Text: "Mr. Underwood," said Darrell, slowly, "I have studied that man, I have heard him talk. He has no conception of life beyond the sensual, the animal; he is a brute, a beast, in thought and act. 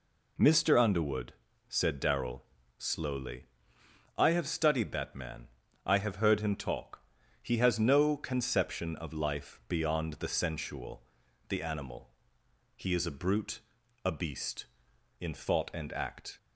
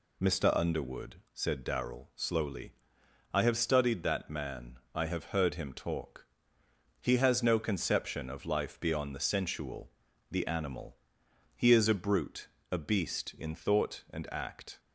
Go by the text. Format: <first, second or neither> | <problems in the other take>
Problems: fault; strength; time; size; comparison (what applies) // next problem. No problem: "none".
neither | none